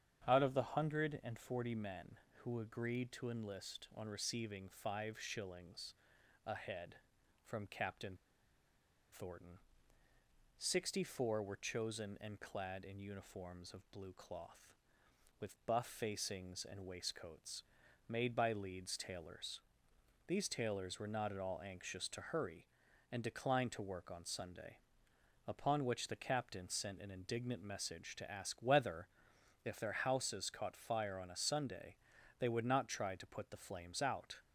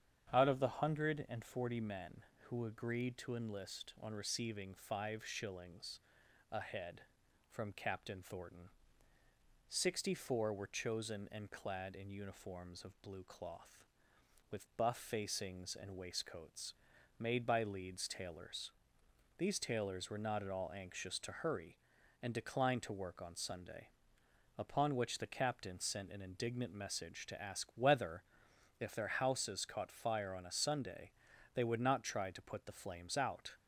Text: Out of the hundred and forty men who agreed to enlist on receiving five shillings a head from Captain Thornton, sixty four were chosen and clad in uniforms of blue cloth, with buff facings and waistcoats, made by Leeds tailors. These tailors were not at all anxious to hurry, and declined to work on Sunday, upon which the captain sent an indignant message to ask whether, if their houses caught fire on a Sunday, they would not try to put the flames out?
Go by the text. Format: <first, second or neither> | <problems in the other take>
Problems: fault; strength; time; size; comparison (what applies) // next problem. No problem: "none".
second | starts louder than the rest; strong; until 1.2 s; 8.5 dB; strong in the second // pauses between "shillings" and "a"; noticeable; at 5.9 s; 0.52 s long; noticeable in the second // pauses between "Captain" and "Thornton"; noticeable; at 8.1 s; 0.97 s long